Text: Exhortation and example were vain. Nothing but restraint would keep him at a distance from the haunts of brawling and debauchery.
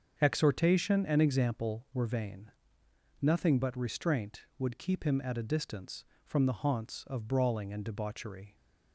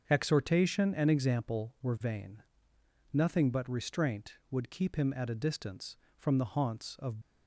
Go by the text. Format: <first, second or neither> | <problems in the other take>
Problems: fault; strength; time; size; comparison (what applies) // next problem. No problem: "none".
first | starts louder than the rest; until 1.0 s; 7 dB; also in the first // stops before "brawling and debauchery"; at 7.2 s